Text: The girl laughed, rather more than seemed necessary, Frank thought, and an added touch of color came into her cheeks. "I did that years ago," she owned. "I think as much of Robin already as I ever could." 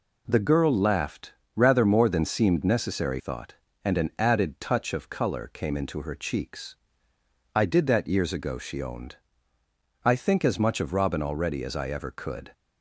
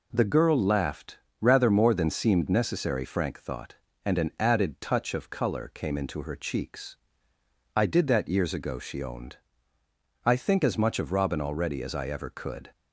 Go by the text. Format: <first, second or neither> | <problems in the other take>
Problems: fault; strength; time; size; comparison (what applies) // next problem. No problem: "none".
second | skips "Frank"; at 3.1 s